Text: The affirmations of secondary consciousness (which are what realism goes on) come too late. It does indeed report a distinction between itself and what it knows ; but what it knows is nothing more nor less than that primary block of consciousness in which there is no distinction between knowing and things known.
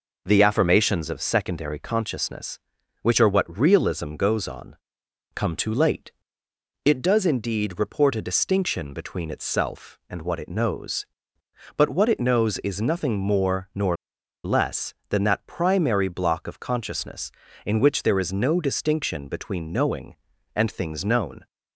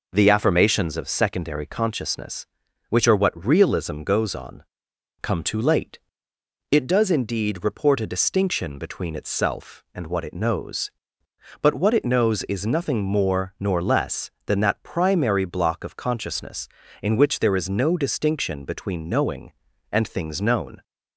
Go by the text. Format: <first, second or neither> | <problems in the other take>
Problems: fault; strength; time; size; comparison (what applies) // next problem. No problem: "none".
second | pauses between "nor" and "less"; noticeable; at 13.9 s; 0.48 s long